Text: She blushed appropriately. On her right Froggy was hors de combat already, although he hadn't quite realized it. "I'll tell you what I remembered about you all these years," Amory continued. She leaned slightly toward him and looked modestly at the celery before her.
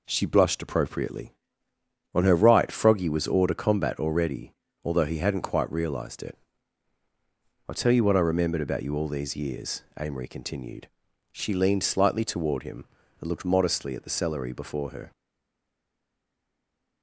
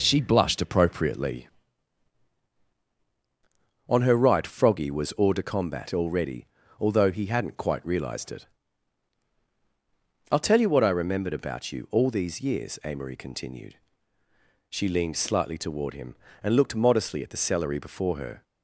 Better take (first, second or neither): second